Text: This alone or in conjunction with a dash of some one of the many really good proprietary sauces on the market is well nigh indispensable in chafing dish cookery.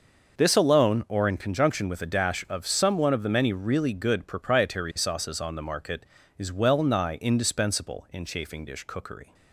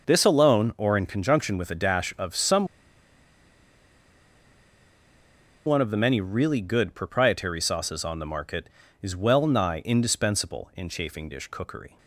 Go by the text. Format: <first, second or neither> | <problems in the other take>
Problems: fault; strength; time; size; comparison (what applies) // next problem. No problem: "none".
first | pauses between "some" and "one"; strong; at 2.6 s; 2.9 s long